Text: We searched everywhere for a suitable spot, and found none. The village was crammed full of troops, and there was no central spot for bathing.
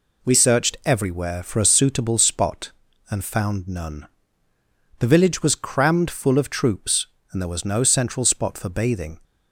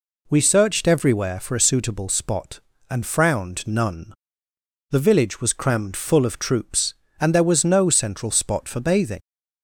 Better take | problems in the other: first | says "frowned" for "found"; at 3.0 s

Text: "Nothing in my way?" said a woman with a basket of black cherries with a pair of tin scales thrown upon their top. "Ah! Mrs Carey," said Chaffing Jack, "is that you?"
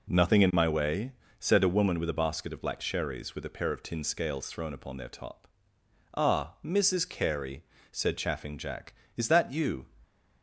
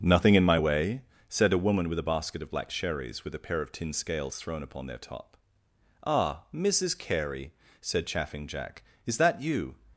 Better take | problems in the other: first | starts louder than the rest; until 1.1 s; 6.5 dB

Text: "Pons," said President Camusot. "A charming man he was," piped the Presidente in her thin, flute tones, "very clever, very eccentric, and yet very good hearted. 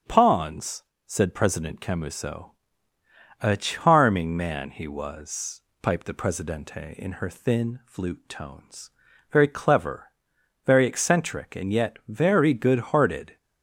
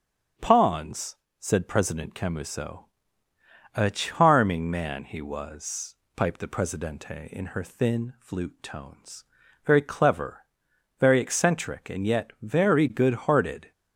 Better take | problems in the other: neither | starts louder than the rest; strong; the same in both

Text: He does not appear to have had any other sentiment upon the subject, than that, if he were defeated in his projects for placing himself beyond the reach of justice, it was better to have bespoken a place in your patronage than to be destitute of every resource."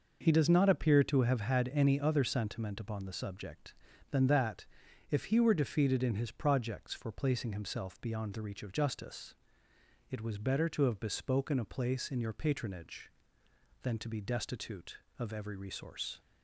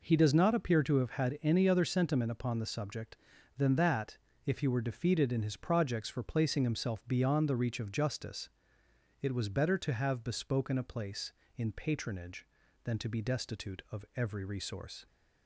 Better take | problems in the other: first | skips "your"; at 11.7 s

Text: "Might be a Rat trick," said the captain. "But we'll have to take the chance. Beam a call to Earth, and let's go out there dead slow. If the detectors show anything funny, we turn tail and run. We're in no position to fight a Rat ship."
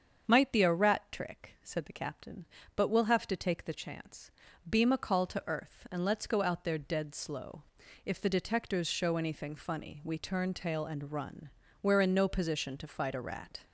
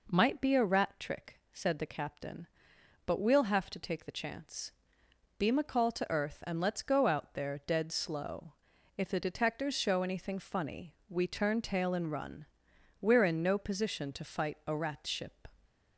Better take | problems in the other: second | starts louder than the rest; strong; until 1.2 s; 7 dB // stops before "ship"; at 13.6 s

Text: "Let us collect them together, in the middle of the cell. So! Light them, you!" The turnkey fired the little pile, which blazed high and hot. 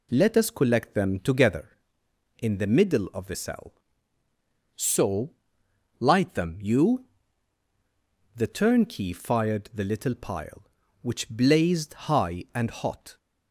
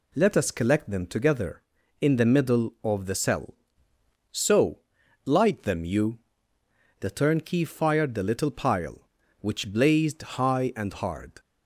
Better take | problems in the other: first | says "hard" for "hot"; at 10.9 s

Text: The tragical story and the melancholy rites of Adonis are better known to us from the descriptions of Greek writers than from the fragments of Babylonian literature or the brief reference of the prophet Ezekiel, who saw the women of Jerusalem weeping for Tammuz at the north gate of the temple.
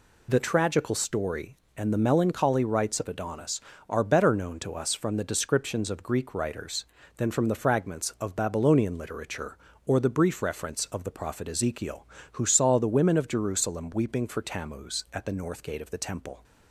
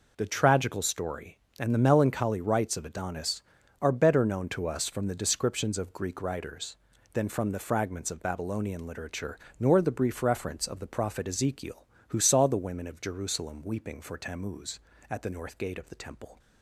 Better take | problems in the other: first | says "nor" for "or"; at 9.5 s

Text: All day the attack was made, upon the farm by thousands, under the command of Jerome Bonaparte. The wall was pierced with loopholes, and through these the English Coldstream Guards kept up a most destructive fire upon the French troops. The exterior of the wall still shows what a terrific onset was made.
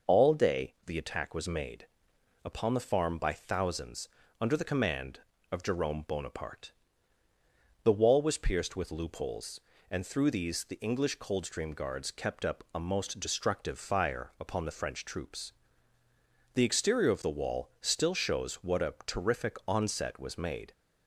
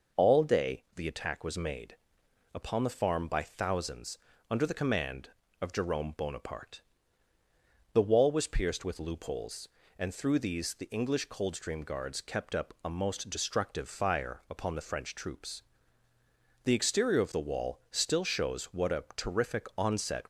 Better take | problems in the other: first | stops before "was made"; at 20.2 s

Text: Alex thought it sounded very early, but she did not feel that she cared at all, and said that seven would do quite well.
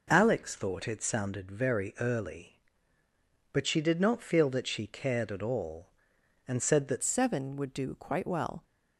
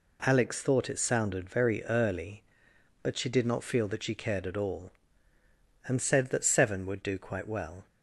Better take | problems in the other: second | changes voice at "seven"; from 7.0 s on; 1.6 s long

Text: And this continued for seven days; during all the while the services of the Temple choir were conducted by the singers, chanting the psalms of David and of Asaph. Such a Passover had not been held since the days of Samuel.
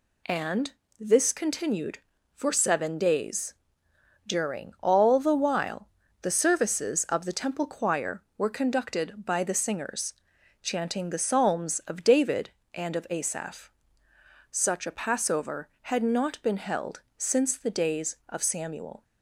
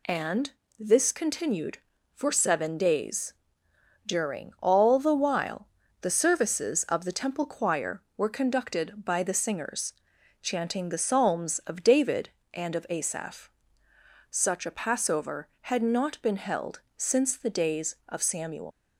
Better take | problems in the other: first | pauses between "And" and "this"; slight; at 0.5 s; 0.28 s long; slight in the first // pauses between "while" and "the"; slight; at 5.6 s; 0.34 s long; slight in the first // leaves "Samuel" unfinished; at 18.7 s; 120 ms

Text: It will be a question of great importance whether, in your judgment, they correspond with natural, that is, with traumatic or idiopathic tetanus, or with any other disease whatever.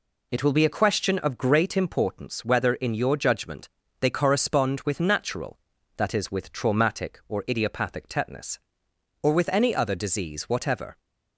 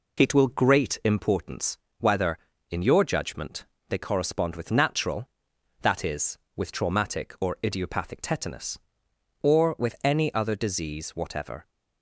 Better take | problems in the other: first | skips "be a question of"; at 0.4 s // pauses between "importance" and "whether"; slight; at 1.7 s; 0.24 s long

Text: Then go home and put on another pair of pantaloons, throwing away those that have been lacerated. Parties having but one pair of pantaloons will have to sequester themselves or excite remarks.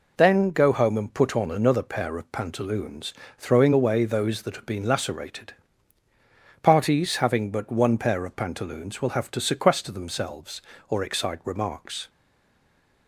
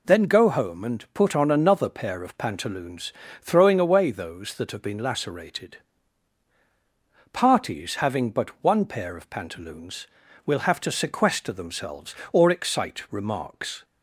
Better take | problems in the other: second | stays silent after the last word; from 12.0 s on; 1.0 s long

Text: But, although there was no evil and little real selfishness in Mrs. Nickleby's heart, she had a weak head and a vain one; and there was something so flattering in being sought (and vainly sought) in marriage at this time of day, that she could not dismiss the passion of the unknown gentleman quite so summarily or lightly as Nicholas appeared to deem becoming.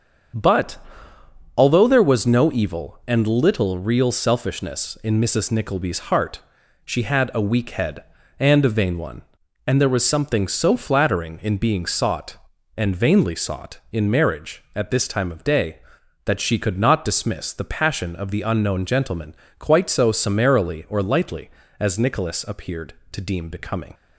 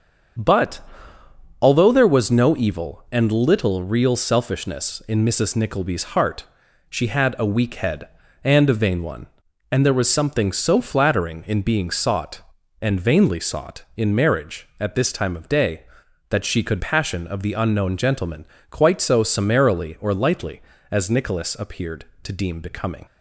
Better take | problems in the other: first | starts louder than the rest; until 2.2 s; 7 dB; also in the first // skips "not dismiss the"; at 16.8 s // pauses between "gentleman" and "quite"; slight; at 18.4 s; 0.24 s long; slight in the first

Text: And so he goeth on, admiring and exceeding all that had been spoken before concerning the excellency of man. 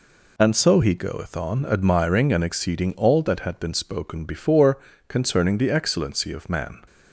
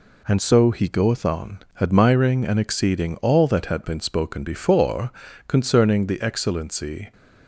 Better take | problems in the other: first | pauses between "before" and "concerning"; at 5.0 s; 0.38 s long; slight in the first // stops before "of man"; at 7.1 s

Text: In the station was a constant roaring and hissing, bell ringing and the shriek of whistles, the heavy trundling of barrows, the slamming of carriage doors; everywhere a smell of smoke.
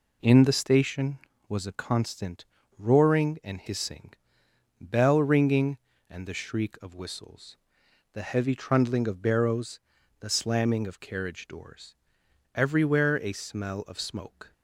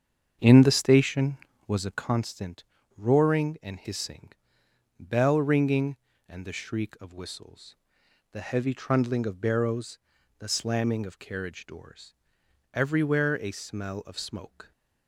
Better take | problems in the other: first | starts louder than the rest; strong; until 2.2 s; 7.5 dB // pauses between "constant" and "roaring"; slight; at 2.6 s; 0.32 s long; slight in the first

